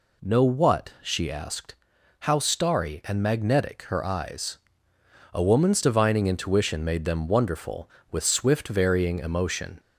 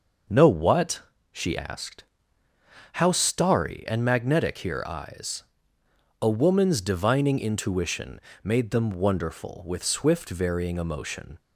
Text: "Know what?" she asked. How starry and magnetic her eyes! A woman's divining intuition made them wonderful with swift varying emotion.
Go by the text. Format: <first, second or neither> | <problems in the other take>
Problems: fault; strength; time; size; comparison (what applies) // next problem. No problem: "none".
first | starts louder than the rest; noticeable; until 1.6 s; 6 dB // says "here" for "her"; at 4.5 s // pauses between "intuition" and "made"; slight; at 8.2 s; 0.20 s long